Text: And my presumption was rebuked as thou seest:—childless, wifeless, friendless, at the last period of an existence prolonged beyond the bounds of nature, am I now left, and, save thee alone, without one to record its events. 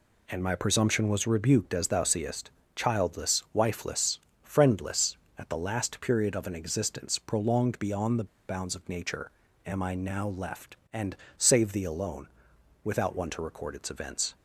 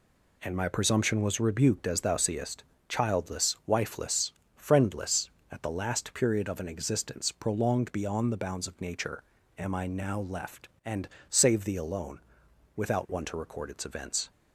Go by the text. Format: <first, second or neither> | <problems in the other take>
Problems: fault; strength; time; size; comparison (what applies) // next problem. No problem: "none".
second | pauses between "the" and "bounds"; slight; at 8.2 s; 0.22 s long